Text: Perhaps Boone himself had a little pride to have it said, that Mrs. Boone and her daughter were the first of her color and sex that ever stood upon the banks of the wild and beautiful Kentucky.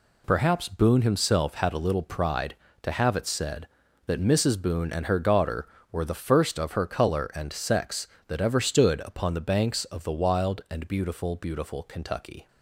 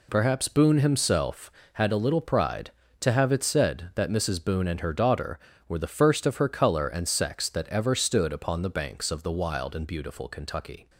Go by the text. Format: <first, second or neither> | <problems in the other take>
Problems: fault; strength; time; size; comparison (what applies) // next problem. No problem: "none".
second | says "beautiful" twice; at 11.3 s